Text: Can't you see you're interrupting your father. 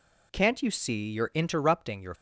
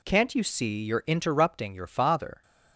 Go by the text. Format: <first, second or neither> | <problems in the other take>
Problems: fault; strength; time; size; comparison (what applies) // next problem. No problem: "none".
second | stops before "father"; at 2.1 s